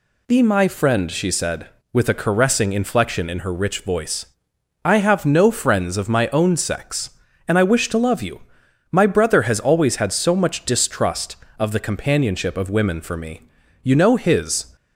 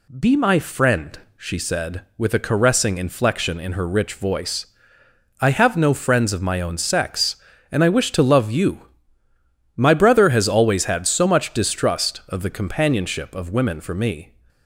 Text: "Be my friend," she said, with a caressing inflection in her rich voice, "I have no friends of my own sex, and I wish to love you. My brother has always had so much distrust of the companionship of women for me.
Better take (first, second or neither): second